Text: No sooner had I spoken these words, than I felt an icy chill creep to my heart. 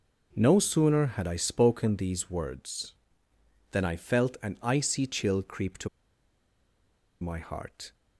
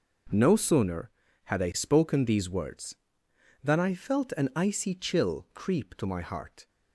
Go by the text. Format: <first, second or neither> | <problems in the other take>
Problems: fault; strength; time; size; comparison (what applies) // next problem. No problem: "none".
second | starts louder than the rest; until 1.4 s; 6.5 dB // pauses between "to" and "my"; strong; at 5.8 s; 1.3 s long